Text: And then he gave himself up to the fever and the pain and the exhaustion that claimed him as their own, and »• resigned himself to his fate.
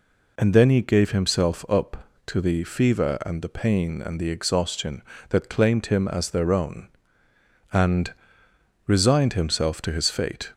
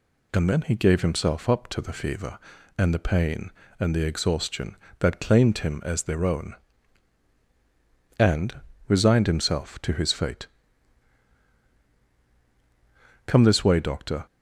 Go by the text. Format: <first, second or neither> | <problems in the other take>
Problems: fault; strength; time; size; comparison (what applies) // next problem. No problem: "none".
first | goes on to say "Come this way doctor"; noticeable; from 13.2 s on; 1.0 s long